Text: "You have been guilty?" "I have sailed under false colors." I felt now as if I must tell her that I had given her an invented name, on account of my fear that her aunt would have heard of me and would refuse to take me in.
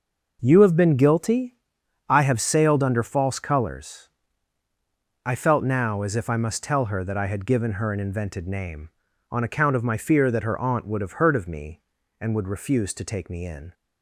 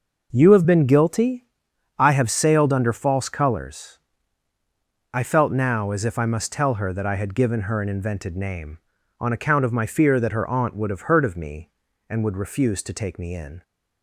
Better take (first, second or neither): neither